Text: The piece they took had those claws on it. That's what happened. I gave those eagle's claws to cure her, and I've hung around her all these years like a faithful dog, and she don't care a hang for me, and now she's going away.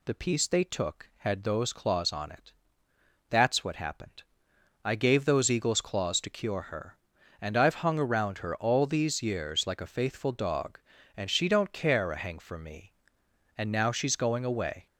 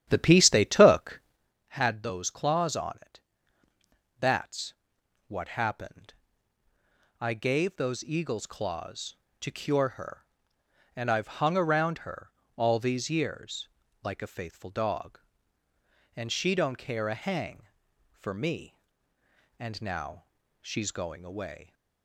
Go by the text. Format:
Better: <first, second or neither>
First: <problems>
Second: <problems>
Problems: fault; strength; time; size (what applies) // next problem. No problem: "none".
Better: first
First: none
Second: starts louder than the rest; strong; until 1.5 s; 10.5 dB // pauses between "That's" and "what"; noticeable; at 4.7 s; 0.54 s long // pauses between "her" and "all"; slight; at 12.3 s; 0.24 s long // pauses between "years" and "like"; slight; at 13.6 s; 0.34 s long // pauses between "now" and "she's"; at 20.2 s; 0.38 s long